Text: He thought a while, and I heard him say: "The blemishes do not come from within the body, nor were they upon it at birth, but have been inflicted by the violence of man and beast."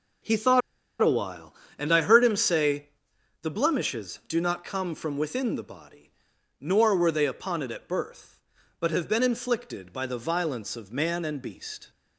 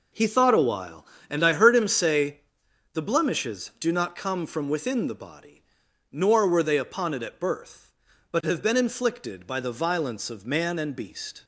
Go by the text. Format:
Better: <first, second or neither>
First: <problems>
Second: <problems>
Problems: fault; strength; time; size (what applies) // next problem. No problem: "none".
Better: second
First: pauses between "thought" and "a"; at 0.6 s; 0.41 s long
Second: none